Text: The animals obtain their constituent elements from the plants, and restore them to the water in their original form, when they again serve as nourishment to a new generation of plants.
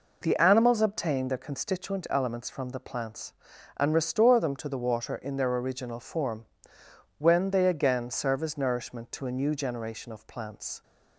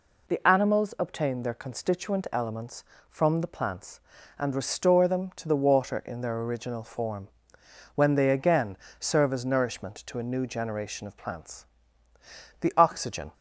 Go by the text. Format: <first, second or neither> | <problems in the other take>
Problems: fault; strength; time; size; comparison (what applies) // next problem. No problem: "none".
first | pauses between "again" and "serve"; slight; at 8.7 s; 0.24 s long // goes on to say "The oxygen"; noticeable; from 12.6 s on; 0.72 s long